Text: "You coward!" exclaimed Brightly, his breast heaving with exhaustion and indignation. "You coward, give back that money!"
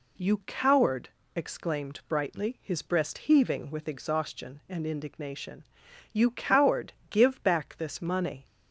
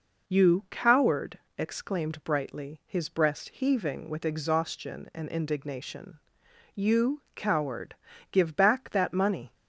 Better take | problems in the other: second | says "this" for "that"; at 7.7 s

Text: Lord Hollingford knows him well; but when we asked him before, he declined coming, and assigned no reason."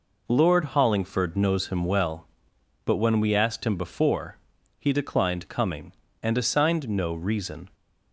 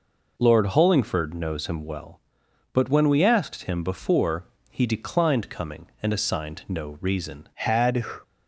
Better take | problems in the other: first | goes on to say "Had"; from 7.5 s on; 0.50 s long

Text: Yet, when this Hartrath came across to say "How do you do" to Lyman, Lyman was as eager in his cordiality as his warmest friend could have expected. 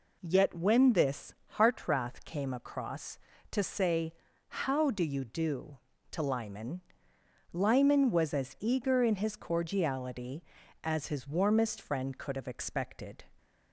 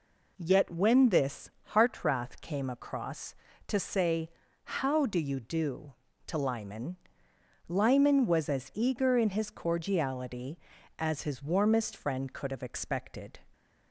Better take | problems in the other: neither | pauses between "this" and "Hartrath"; slight; the same in both // pauses between "say" and "How"; slight; the same in both

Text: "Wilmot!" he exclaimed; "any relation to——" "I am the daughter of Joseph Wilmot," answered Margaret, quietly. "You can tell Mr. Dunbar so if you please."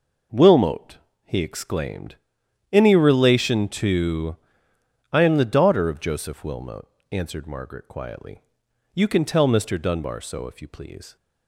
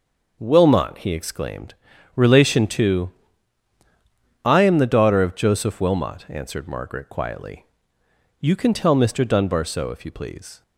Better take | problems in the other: first | starts louder than the rest; noticeable; until 1.4 s; 6 dB // skips "any"; at 1.9 s

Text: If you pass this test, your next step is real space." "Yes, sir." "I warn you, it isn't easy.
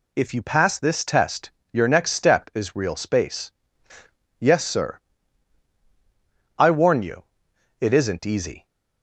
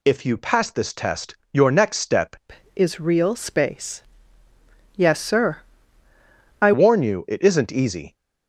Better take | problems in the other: first | changes voice from "is" to "I"; from 2.7 to 6.7 s; 4.0 s long

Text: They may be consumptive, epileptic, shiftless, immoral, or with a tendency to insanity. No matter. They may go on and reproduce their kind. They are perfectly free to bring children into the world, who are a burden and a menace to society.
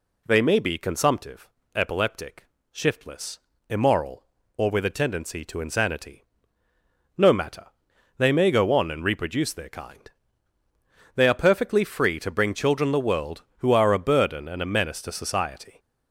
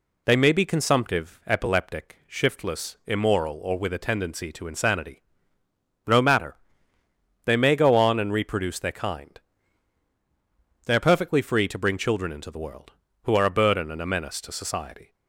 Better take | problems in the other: second | skips "into"; at 12.9 s

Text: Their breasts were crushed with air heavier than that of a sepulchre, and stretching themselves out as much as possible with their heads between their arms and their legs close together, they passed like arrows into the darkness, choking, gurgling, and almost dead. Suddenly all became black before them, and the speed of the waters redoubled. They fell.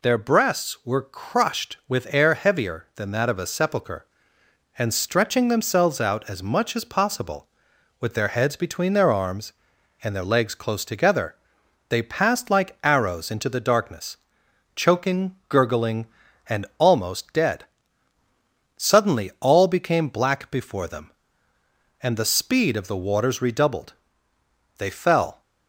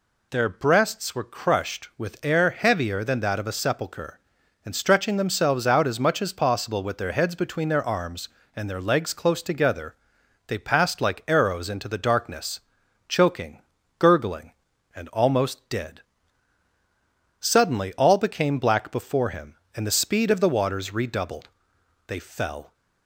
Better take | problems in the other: first | says "him" for "them"; at 19.2 s

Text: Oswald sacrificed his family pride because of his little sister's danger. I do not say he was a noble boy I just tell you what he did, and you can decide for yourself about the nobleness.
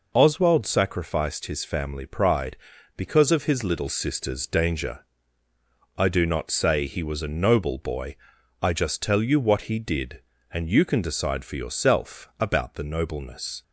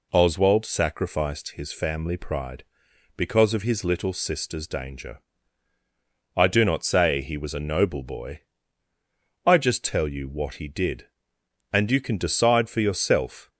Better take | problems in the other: first | pauses between "boy" and "I"; at 8.4 s; 1.0 s long; noticeable in the first // stops before "about the nobleness"; at 13.4 s

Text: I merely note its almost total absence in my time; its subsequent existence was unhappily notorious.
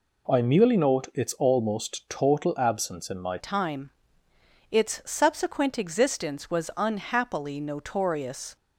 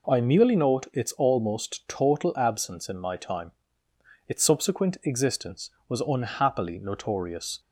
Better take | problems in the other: second | changes voice at "time"; from 3.3 s on; 5.2 s long

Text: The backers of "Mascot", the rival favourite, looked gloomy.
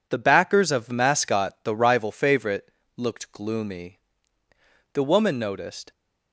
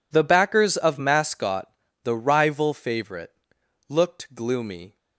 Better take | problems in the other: second | goes on to say "The woman noticed"; noticeable; from 4.9 s on; 0.98 s long

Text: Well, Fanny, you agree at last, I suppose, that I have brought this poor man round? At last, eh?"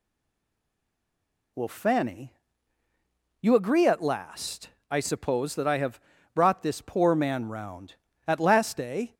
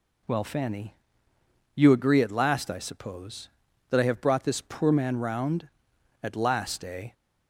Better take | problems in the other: second | stays silent before the first word; noticeable; until 1.5 s; 1.5 s long // pauses between "have" and "brought"; slight; at 5.9 s; 0.34 s long

